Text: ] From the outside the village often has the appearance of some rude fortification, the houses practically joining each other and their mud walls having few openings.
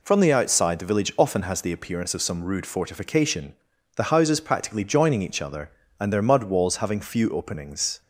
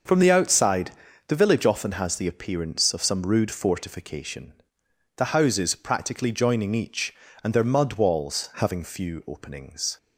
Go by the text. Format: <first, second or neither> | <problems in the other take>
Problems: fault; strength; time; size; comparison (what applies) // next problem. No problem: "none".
first | pauses between "outside" and "the"; slight; at 0.9 s; 0.34 s long // skips "other"; at 7.2 s